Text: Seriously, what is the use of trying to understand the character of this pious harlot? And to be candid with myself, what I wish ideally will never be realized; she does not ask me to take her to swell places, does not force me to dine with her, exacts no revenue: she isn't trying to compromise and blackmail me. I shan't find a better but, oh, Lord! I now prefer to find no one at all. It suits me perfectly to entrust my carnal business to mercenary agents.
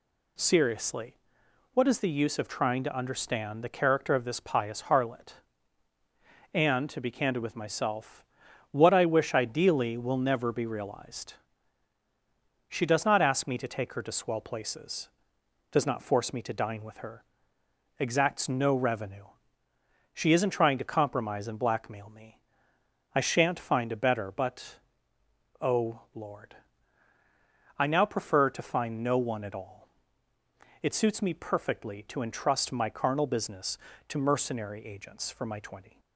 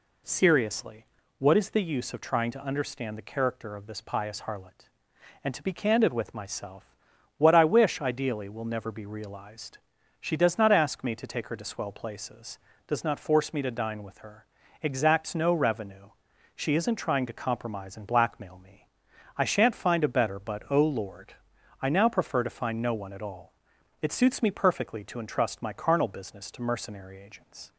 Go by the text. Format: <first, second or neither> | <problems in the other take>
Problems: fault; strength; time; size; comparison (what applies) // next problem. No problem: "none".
second | goes on to say "For my twenty"; noticeable; from 35.3 s on; 0.68 s long